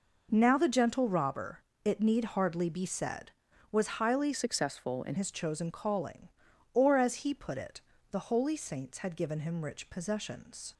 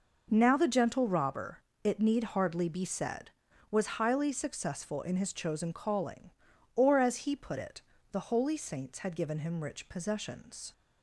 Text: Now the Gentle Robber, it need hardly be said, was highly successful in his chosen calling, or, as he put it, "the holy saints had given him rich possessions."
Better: second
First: changes voice from "successful" to "in"; from 4.3 to 5.1 s; 0.8 s long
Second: none

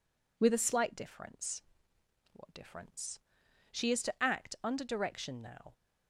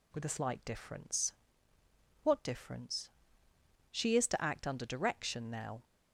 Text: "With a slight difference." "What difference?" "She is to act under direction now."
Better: neither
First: none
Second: none

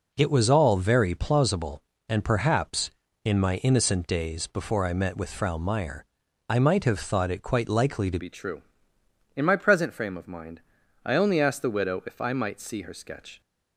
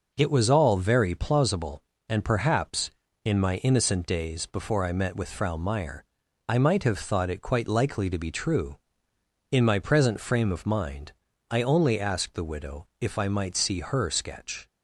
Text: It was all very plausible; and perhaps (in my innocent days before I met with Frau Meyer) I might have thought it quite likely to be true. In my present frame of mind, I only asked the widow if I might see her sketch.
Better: second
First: changes voice at "be"; from 8.1 s on; 5.3 s long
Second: none

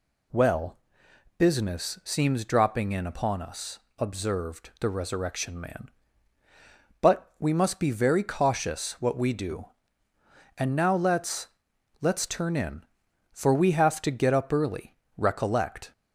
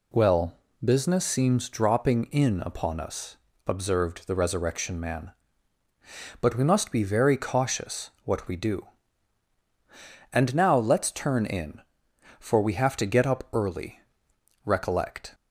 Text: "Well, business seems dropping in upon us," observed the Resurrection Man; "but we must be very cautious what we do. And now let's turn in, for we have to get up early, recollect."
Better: second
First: says "let's" twice; at 11.9 s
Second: none

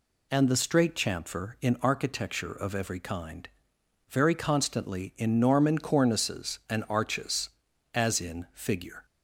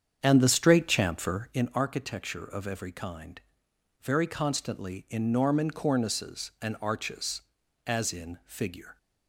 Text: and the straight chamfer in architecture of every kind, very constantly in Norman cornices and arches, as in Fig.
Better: first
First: none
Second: starts louder than the rest; strong; until 1.6 s; 8 dB

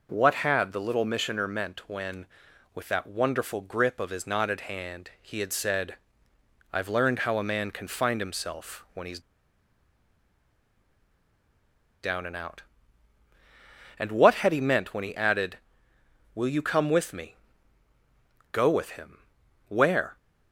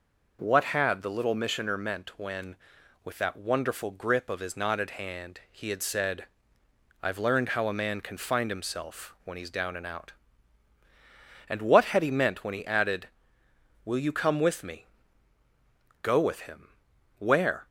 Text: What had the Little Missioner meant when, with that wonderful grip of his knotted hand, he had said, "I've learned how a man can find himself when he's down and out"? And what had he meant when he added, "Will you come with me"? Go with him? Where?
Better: second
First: pauses between "he's" and "down"; strong; at 9.2 s; 2.8 s long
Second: none

